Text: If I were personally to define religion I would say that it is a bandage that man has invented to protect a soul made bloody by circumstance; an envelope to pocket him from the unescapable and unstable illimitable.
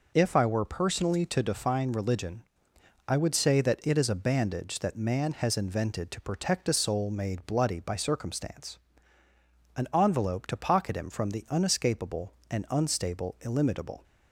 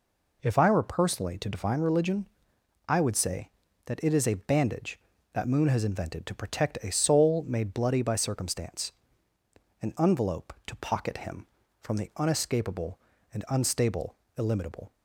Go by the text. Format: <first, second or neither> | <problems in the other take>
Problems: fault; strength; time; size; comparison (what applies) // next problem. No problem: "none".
first | pauses between "religion" and "I"; noticeable; at 2.2 s; 0.62 s long; noticeable in the first // says "moon" for "man"; at 5.4 s // pauses between "unstable" and "illimitable"; slight; at 14.1 s; 0.22 s long